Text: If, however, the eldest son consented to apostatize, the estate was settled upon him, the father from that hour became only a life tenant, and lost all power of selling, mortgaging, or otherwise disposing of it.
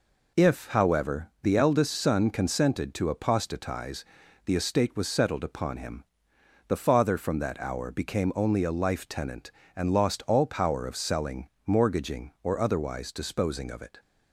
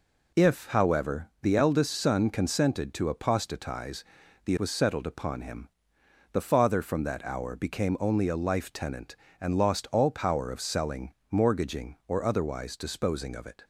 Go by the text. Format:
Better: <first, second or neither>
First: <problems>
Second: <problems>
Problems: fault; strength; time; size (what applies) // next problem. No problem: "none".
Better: first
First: none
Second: skips "estate"; at 4.5 s